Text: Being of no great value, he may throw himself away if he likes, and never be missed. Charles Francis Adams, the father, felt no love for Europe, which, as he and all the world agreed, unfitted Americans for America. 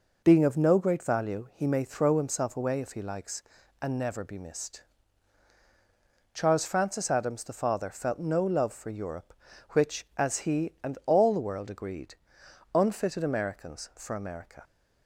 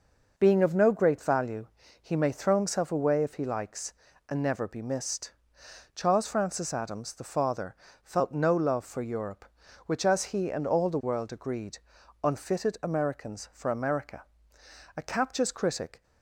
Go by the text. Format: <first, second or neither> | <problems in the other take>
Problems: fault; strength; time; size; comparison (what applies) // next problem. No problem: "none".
first | goes on to say "A captious critic"; noticeable; from 14.9 s on; 1.0 s long